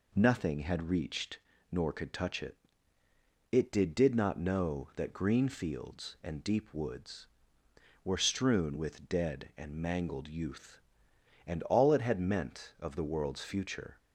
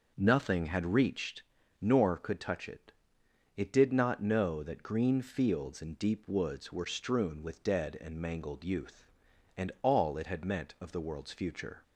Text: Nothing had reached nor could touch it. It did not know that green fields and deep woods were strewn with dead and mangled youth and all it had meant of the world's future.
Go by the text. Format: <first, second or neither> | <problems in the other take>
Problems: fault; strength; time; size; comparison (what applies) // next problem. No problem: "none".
second | pauses between "reached" and "nor"; slight; at 1.3 s; 0.32 s long; also in the second // says "did" twice; at 3.9 s